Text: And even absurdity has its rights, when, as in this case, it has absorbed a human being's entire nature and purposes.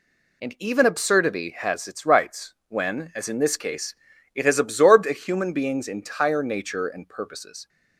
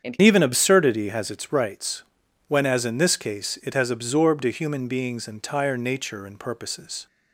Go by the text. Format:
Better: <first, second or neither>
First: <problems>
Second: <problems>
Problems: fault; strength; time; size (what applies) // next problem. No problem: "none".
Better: first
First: none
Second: starts louder than the rest; strong; until 1.1 s; 7.5 dB // changes voice at "even"; from 0.2 s on; 6.8 s long